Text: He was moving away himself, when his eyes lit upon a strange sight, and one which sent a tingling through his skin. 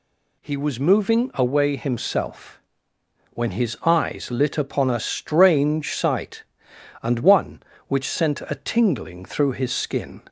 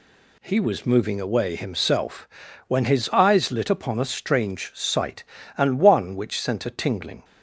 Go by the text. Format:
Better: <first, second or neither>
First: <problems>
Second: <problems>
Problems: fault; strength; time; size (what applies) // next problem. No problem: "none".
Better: first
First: none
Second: stops before "through his skin"; at 7.2 s